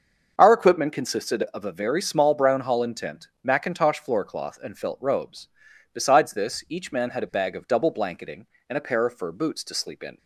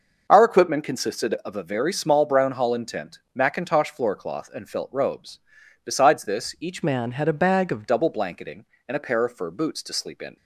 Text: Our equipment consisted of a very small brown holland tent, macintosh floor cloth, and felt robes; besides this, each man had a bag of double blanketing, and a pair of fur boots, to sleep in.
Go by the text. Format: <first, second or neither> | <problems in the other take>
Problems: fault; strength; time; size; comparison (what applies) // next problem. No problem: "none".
first | starts louder than the rest; noticeable; until 1.3 s; 6 dB; also in the first // changes voice from "man" to "of"; from 6.8 to 7.8 s; 1.0 s long